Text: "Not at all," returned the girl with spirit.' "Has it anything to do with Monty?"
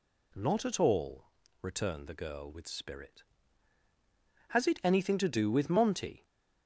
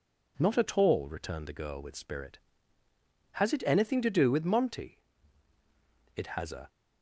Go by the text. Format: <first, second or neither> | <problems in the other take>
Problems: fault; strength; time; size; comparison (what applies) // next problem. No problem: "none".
first | goes on to say "It has a"; from 6.1 s on; 0.54 s long